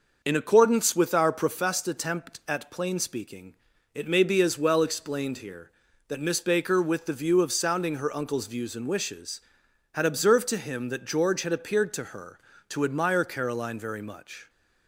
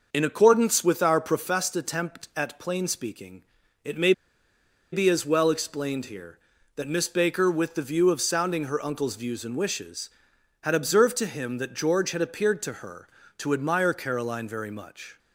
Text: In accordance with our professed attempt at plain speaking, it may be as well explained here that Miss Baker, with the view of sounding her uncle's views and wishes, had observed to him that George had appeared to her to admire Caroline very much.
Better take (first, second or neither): first